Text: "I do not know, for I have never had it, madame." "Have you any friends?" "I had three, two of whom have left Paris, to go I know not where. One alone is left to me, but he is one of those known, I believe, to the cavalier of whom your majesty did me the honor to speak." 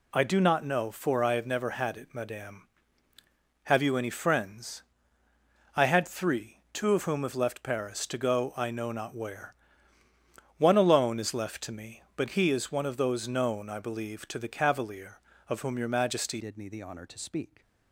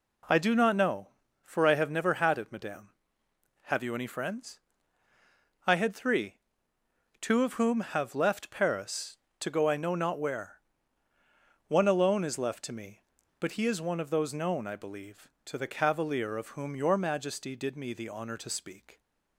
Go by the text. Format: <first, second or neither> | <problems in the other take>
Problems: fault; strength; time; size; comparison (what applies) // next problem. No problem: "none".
second | changes voice at "did"; from 16.3 s on; 1.3 s long